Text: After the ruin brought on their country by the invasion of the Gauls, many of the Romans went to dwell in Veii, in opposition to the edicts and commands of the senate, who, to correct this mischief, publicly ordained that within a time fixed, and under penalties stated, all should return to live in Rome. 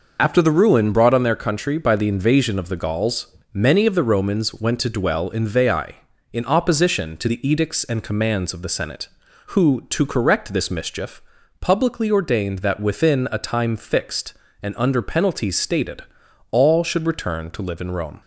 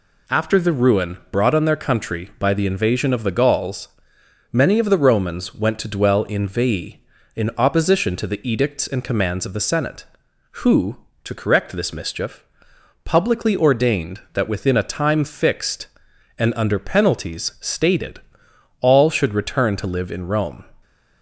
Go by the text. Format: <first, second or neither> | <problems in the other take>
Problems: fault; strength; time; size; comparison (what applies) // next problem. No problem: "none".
second | loses the start of "After"; at 0.1 s; 80 ms